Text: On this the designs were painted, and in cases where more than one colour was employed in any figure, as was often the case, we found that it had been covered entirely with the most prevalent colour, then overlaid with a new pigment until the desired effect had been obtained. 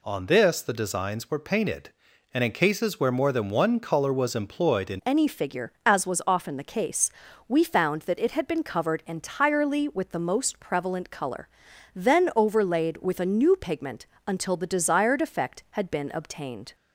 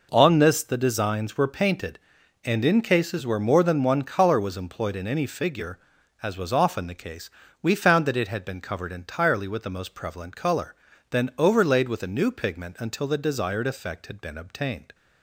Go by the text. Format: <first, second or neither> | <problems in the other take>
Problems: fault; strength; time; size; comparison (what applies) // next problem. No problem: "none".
second | changes voice at "any"; from 5.0 s on; 11.7 s long // pauses between "pigment" and "until"; slight; at 14.0 s; 0.22 s long